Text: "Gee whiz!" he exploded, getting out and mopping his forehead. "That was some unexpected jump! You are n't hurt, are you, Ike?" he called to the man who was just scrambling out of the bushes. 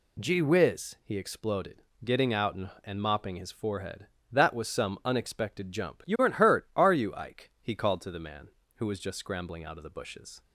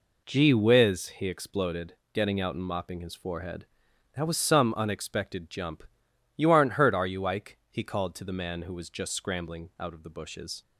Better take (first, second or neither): second